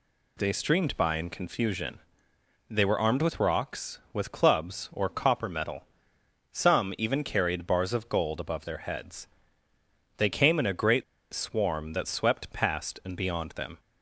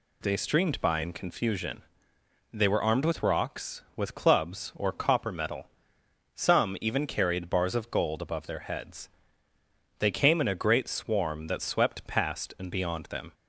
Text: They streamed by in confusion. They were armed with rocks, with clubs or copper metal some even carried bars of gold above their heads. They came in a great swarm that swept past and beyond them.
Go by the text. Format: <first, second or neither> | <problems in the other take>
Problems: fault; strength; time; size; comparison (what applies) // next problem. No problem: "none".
second | pauses between "metal" and "some"; noticeable; at 5.8 s; 0.66 s long; noticeable in the second // pauses between "great" and "swarm"; slight; at 11.0 s; 0.29 s long